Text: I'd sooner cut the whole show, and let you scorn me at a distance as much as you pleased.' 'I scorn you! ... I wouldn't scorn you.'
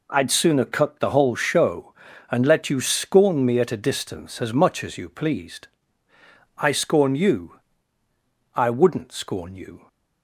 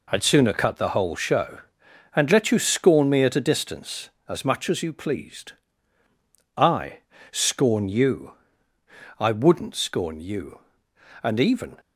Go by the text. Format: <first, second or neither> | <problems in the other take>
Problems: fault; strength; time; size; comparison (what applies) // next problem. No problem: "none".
first | pauses between "I" and "scorn"; slight; at 6.9 s; 0.32 s long // goes on to say "And even"; from 11.2 s on; 0.58 s long